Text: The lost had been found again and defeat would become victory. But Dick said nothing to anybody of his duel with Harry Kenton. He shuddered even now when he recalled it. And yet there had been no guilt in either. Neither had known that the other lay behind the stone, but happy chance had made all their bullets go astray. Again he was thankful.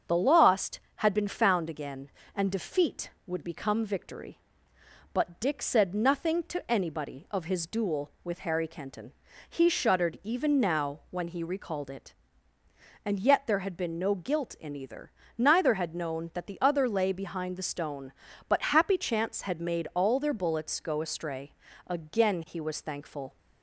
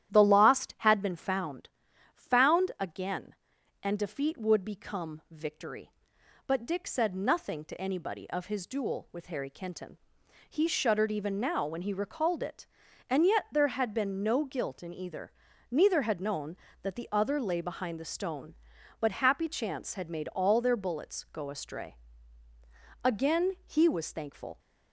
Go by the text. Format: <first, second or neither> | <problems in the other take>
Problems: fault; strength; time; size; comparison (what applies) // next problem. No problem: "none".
first | starts louder than the rest; strong; until 1.1 s; 11.5 dB; also in the first // says "found" twice; at 2.1 s